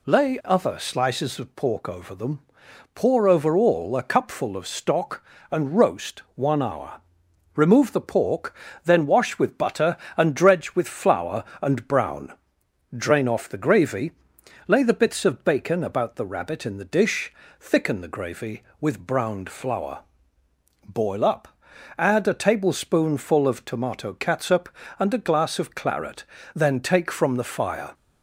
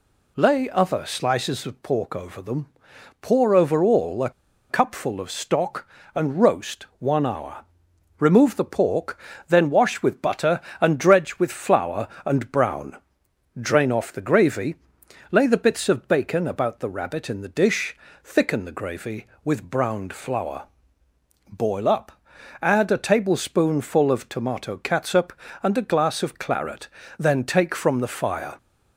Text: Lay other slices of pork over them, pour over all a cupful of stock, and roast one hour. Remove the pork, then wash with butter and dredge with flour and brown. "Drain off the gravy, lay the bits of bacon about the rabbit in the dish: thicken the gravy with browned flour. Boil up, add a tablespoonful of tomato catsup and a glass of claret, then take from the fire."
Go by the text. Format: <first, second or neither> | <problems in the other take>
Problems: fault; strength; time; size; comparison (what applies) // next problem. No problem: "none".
first | pauses between "a" and "cupful"; at 4.3 s; 0.39 s long